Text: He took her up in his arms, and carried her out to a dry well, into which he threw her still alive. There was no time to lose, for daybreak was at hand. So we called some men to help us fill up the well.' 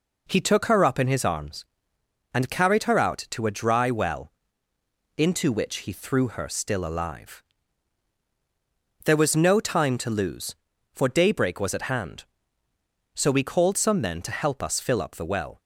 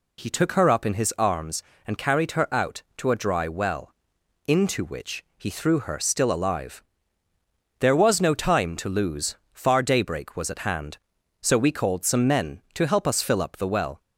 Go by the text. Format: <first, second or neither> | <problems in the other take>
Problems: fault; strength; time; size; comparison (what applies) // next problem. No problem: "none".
first | says "far" for "for"; at 9.5 s